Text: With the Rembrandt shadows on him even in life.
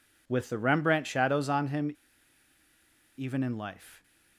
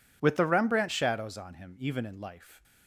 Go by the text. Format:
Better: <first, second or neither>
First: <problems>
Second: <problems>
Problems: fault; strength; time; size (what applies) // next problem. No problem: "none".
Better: second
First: pauses between "him" and "even"; at 1.9 s; 1.2 s long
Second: none